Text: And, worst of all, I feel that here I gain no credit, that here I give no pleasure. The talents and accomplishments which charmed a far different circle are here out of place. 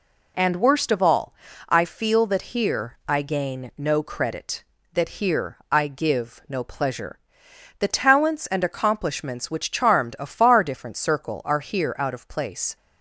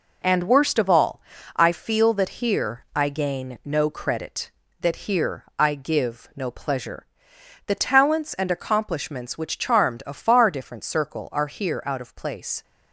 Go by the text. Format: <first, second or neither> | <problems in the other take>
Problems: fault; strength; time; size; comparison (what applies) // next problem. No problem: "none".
first | gets quieter; throughout; 6.5 dB